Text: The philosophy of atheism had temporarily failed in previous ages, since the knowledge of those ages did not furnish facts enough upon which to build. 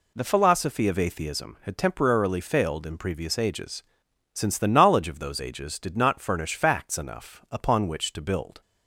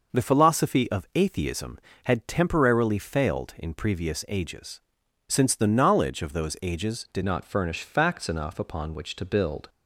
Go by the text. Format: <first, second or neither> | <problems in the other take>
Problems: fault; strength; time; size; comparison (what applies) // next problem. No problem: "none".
first | changes voice at "not"; from 7.2 s on; 2.4 s long